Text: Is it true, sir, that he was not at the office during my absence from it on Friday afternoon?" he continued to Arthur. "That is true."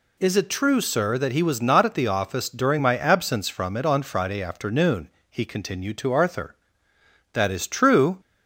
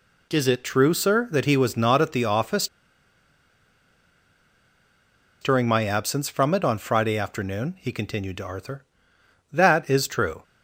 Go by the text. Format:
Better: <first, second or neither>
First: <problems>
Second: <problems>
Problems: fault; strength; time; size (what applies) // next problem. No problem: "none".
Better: first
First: none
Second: pauses between "office" and "during"; strong; at 2.6 s; 2.7 s long